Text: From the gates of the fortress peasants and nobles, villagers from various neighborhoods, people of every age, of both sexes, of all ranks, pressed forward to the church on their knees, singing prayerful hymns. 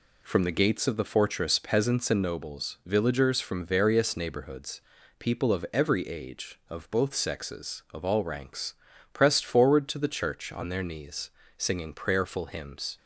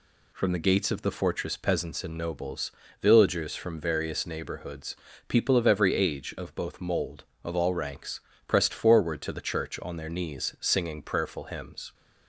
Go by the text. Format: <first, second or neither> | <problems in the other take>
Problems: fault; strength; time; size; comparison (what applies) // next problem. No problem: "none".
first | says "mold" for "sexes"; at 6.8 s